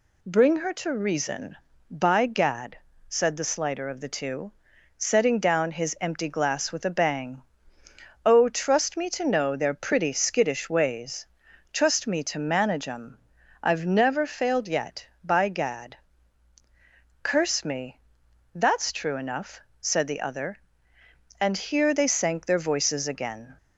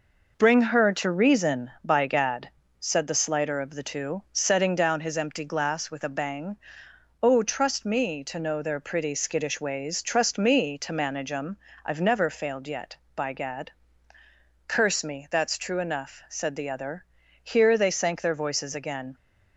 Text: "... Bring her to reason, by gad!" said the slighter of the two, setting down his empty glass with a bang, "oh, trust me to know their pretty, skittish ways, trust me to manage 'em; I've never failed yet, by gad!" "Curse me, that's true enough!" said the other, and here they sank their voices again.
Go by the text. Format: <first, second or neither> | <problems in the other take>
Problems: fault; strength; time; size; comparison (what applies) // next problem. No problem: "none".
first | skips "and"; at 17.2 s